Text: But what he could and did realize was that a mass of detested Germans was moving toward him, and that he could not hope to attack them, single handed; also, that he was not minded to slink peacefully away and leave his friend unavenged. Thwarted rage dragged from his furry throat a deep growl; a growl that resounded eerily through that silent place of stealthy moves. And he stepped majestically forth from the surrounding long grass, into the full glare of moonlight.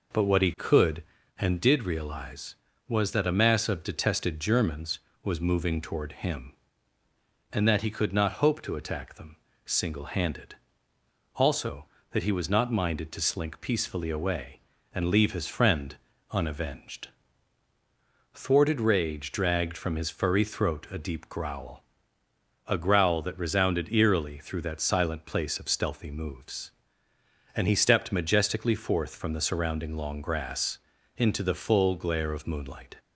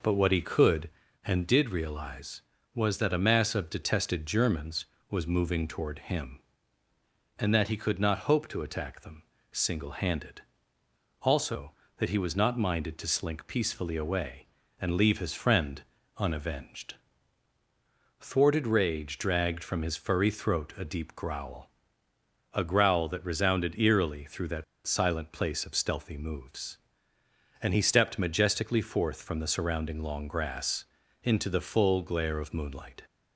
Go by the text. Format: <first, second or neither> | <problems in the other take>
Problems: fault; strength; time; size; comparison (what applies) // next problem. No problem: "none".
first | pauses between "friend" and "unavenged"; slight; at 15.8 s; 0.34 s long; slight in the first // pauses between "that" and "silent"; slight; at 24.6 s; 0.23 s long